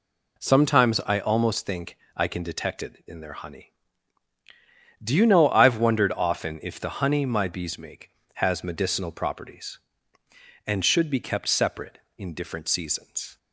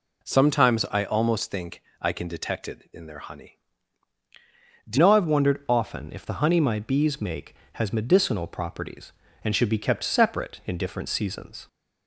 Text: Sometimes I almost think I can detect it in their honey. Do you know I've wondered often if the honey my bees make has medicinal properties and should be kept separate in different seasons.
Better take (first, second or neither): first